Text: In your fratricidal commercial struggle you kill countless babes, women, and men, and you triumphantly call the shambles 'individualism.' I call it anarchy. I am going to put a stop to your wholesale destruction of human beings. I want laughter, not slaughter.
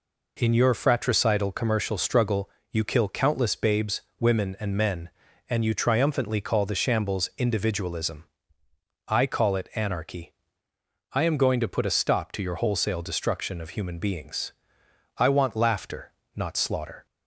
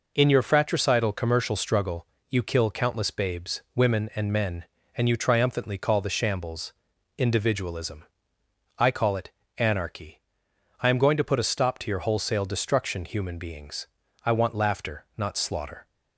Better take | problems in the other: first | pauses between "struggle" and "you"; slight; at 2.0 s; 0.26 s long; slight in the first // pauses between "shambles" and "individualism"; at 6.7 s; 0.44 s long // pauses between "it" and "anarchy"; slight; at 9.2 s; 0.28 s long // skips "of"; at 13.0 s

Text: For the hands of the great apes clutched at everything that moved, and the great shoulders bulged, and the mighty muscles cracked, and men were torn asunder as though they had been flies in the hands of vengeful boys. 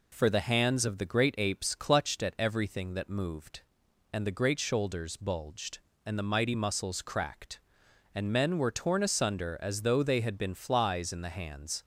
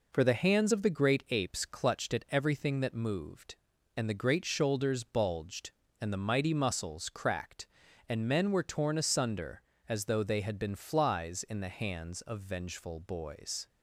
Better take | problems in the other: second | stops before "of vengeful boys"; at 11.8 s

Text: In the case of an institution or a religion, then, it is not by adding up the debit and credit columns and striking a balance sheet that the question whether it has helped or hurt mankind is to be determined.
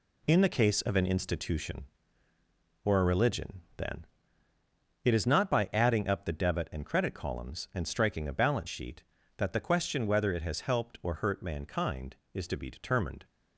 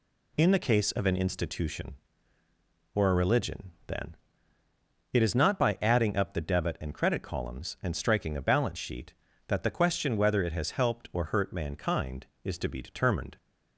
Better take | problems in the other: second | gets quieter; throughout; 7 dB

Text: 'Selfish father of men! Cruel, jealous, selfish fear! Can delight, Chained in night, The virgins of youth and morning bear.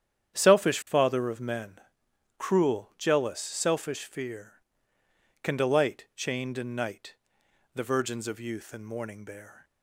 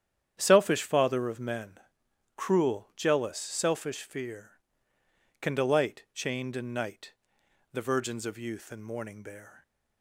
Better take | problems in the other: neither | starts louder than the rest; strong; the same in both

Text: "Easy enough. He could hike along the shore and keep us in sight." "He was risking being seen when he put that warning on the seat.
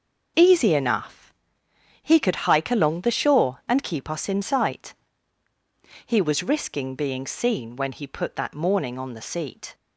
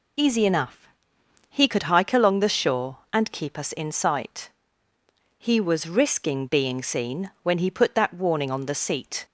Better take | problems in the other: second | says "morning" for "warning"; at 8.5 s

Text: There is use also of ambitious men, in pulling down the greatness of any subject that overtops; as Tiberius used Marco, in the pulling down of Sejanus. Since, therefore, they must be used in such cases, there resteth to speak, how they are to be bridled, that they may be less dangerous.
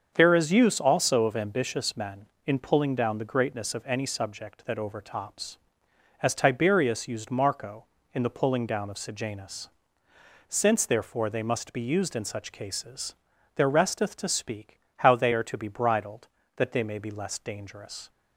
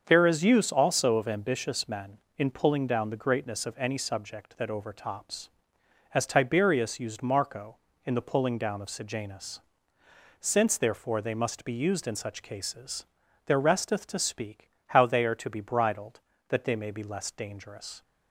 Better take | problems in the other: neither | starts louder than the rest; the same in both

